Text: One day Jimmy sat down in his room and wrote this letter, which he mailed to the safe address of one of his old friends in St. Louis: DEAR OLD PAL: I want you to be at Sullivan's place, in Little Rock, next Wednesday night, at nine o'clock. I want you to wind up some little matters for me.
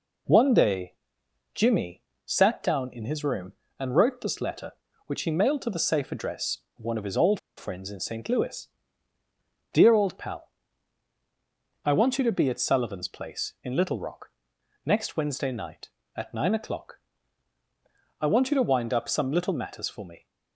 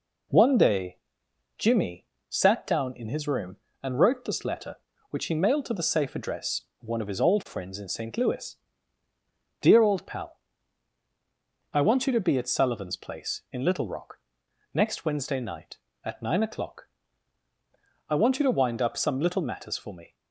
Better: second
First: pauses between "day" and "Jimmy"; noticeable; at 0.9 s; 0.60 s long // pauses between "Jimmy" and "sat"; slight; at 2.0 s; 0.22 s long // pauses between "old" and "friends"; slight; at 7.3 s; 0.19 s long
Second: pauses between "day" and "Jimmy"; noticeable; at 0.9 s; 0.60 s long // pauses between "Jimmy" and "sat"; slight; at 2.0 s; 0.22 s long

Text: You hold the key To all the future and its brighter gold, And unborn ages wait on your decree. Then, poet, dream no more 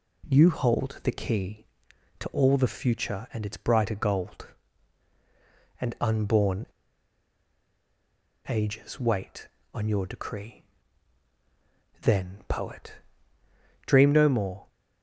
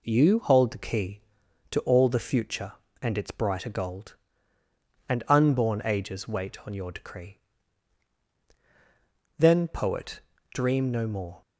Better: second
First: pauses between "unborn" and "ages"; strong; at 6.6 s; 1.8 s long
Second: none

